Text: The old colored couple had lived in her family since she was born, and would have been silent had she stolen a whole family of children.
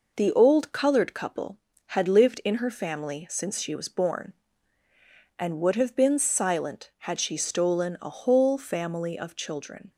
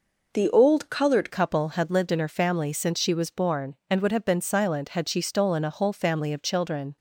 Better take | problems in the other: first | changes voice at "couple"; from 1.2 s on; 5.7 s long

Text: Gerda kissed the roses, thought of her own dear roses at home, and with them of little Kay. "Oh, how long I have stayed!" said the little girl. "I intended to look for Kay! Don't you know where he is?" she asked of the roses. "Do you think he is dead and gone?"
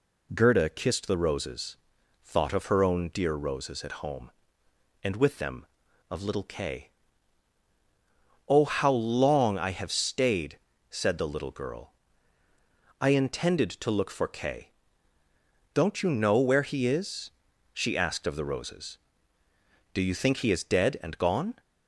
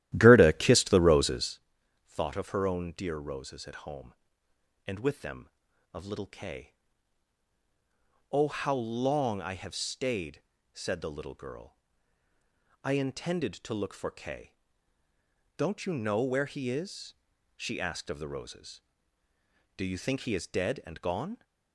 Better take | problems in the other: first | starts louder than the rest; strong; until 1.5 s; 14 dB

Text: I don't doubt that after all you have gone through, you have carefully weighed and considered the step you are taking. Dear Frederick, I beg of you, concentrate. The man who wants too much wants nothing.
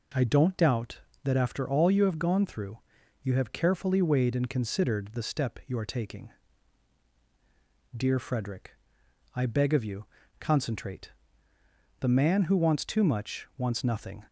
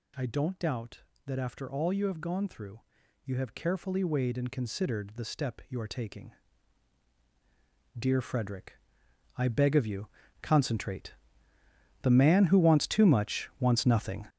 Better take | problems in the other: first | gets louder; strong; throughout; 8.5 dB

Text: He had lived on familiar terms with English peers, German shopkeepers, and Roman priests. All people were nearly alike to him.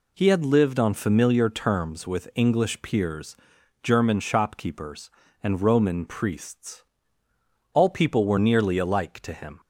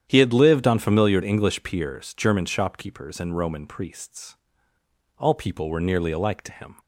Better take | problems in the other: first | starts louder than the rest; strong; until 1.0 s; 9.5 dB // skips "terms with"; at 1.2 s

